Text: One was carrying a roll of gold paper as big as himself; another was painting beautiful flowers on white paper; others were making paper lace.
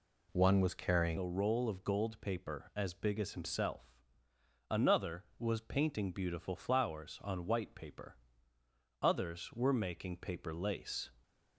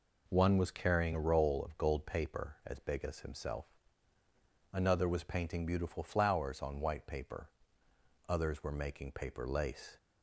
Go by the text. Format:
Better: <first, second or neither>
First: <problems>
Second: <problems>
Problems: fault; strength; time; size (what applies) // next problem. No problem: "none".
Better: second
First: changes voice at "a"; from 1.1 s on; 10.0 s long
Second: none